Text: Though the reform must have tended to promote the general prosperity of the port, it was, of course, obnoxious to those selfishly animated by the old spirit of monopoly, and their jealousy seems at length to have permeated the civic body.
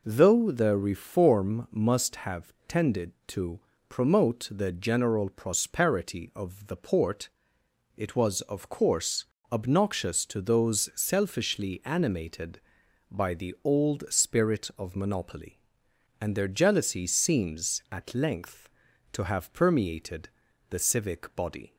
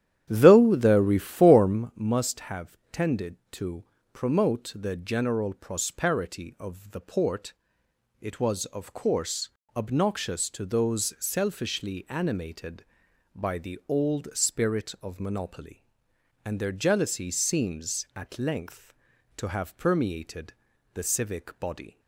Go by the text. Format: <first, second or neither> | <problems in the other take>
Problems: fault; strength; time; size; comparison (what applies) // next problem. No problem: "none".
first | starts louder than the rest; strong; until 1.9 s; 11 dB // pauses between "have" and "tended"; slight; at 2.7 s; 0.16 s long; slight in the first // pauses between "to" and "promote"; slight; at 3.8 s; 0.26 s long; slight in the first // pauses between "permeated" and "the"; at 20.5 s; 0.42 s long; also in the first